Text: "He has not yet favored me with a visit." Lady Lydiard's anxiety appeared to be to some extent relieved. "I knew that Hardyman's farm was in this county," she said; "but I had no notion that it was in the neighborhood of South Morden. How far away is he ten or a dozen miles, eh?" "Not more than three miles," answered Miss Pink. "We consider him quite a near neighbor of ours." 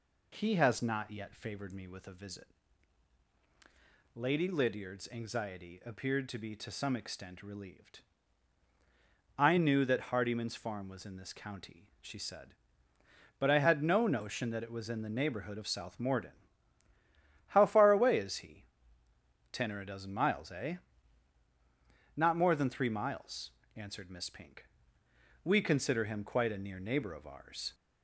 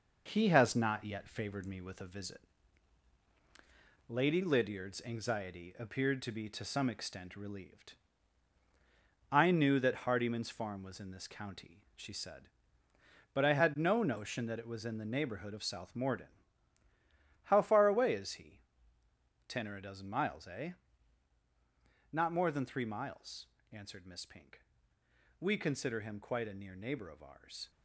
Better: first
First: pauses between "he" and "ten"; noticeable; at 18.6 s; 0.88 s long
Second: gets quieter; noticeable; throughout; 5 dB // pauses between "he" and "ten"; noticeable; at 18.5 s; 0.88 s long

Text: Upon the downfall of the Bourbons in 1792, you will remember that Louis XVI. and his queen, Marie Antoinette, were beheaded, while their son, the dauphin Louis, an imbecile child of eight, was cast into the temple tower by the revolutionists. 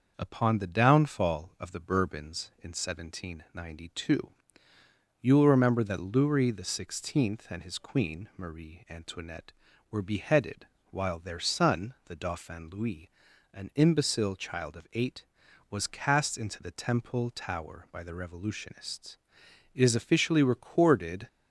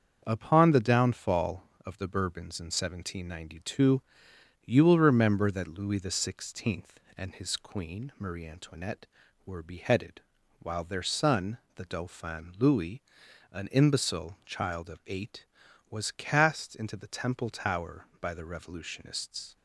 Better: second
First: starts louder than the rest; until 1.1 s; 6 dB // goes on to say "It is officially recorded"; from 19.7 s on; 1.5 s long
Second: starts louder than the rest; until 1.2 s; 7 dB

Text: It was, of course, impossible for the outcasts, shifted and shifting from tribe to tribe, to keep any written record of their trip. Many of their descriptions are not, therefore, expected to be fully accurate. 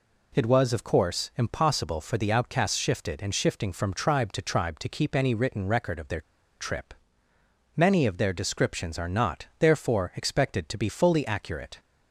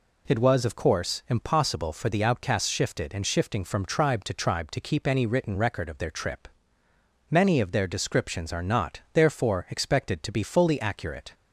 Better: second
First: pauses between "their" and "trip"; at 6.2 s; 0.37 s long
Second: none

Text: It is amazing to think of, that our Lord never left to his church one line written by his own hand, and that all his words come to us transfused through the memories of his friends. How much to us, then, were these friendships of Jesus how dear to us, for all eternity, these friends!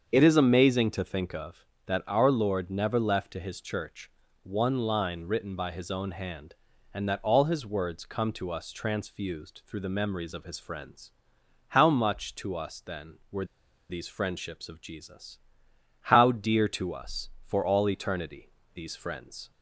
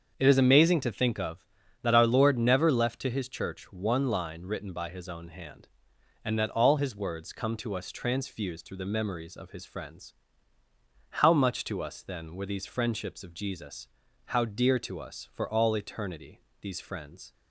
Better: second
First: starts louder than the rest; until 1.1 s; 7 dB // pauses between "church" and "one"; slight; at 4.0 s; 0.32 s long // pauses between "were" and "these"; at 13.4 s; 0.45 s long // pauses between "Jesus" and "how"; noticeable; at 15.3 s; 0.66 s long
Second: starts louder than the rest; until 1.1 s; 7 dB // pauses between "Jesus" and "how"; at 13.8 s; 0.40 s long

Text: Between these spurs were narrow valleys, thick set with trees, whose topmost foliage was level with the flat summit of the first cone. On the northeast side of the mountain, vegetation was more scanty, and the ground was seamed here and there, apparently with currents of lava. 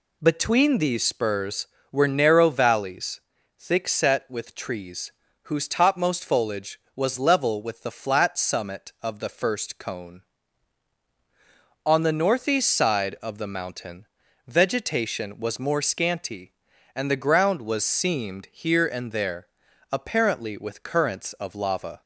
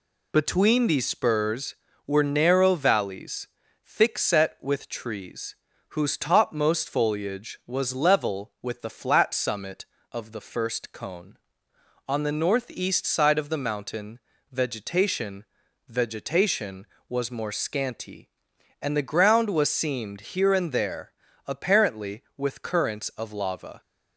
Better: first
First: none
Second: says "vegetation" twice; at 15.8 s

